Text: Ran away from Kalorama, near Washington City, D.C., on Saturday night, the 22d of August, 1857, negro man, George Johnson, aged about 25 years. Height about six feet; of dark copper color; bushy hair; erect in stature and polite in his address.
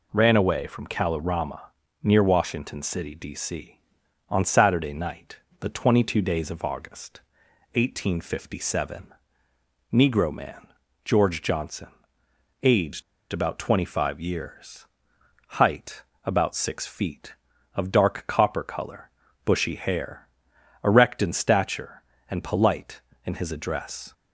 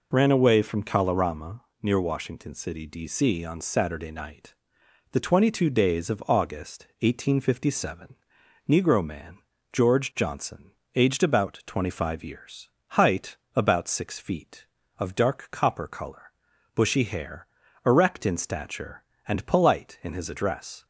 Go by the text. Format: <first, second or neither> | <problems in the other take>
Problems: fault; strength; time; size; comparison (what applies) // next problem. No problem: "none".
second | pauses between "aged" and "about"; slight; at 13.0 s; 0.30 s long // pauses between "Height" and "about"; slight; at 16.0 s; 0.20 s long; slight in the second